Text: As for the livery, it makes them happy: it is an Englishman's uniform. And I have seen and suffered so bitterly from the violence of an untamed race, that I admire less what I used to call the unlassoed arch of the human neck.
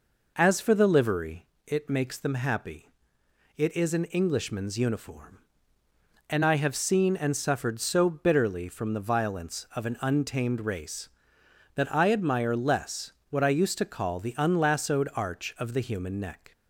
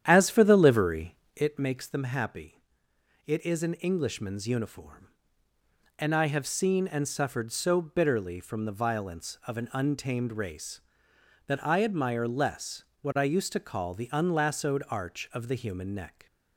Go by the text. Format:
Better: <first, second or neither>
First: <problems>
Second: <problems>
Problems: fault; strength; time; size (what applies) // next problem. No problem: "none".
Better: first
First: pauses between "less" and "what"; slight; at 13.1 s; 0.20 s long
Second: starts louder than the rest; strong; until 1.7 s; 10 dB // pauses between "less" and "what"; slight; at 12.8 s; 0.20 s long